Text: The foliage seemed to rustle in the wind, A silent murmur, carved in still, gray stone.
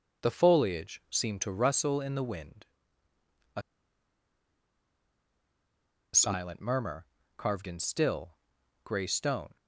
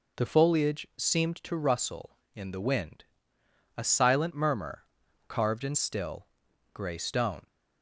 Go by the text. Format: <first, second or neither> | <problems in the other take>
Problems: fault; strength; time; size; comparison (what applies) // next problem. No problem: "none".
second | pauses between "A" and "silent"; strong; at 3.6 s; 2.5 s long